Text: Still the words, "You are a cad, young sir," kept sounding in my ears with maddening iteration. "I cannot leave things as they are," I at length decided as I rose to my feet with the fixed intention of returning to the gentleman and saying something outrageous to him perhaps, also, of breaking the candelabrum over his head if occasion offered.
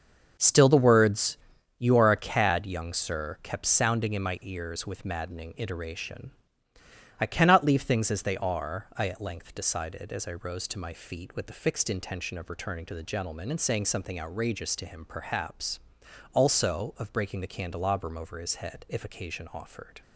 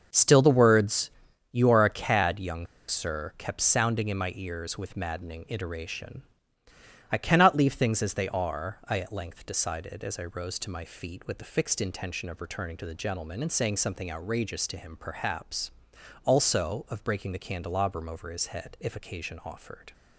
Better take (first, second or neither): first